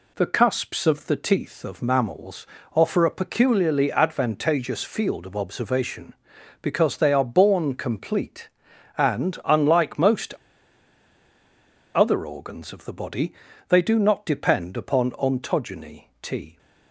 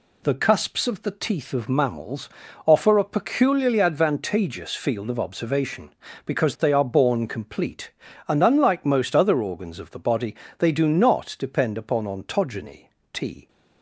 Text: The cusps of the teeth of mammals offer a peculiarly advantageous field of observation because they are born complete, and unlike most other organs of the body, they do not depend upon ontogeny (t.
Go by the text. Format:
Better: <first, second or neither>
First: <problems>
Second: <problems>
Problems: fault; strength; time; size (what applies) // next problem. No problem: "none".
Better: second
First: pauses between "mammals" and "offer"; slight; at 2.4 s; 0.30 s long // pauses between "most" and "other"; strong; at 10.3 s; 1.6 s long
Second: pauses between "mammals" and "offer"; slight; at 2.2 s; 0.36 s long